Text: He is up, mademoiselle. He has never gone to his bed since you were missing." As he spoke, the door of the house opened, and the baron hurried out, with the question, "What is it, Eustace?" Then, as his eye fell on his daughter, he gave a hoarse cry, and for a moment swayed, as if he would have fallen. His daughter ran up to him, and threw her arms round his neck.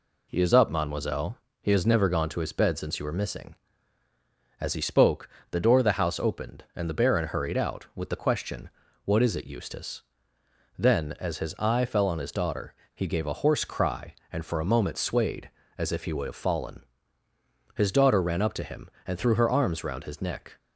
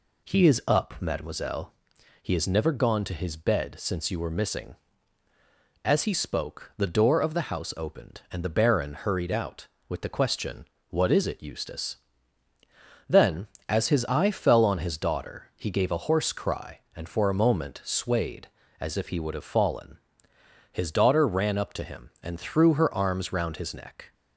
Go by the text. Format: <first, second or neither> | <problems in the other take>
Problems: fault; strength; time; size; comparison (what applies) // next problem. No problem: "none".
neither | none